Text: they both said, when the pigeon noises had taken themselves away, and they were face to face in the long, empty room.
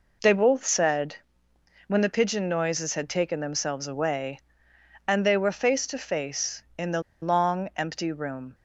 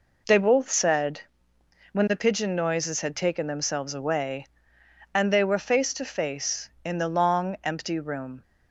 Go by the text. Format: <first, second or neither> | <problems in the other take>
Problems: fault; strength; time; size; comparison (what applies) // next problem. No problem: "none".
second | pauses between "the" and "long"; slight; at 7.0 s; 0.20 s long